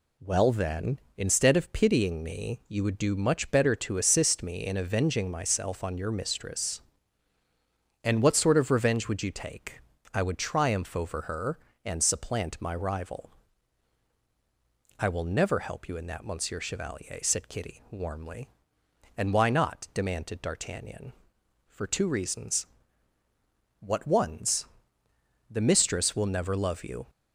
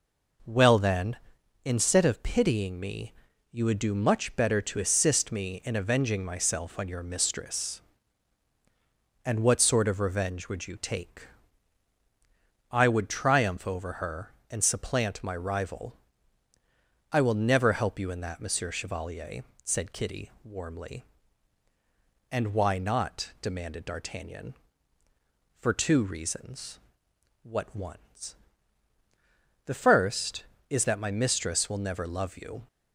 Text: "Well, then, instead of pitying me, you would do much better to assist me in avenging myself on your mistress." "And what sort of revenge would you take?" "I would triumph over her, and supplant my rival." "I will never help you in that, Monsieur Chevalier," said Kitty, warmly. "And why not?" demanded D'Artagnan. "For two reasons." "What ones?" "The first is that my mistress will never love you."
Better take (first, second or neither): second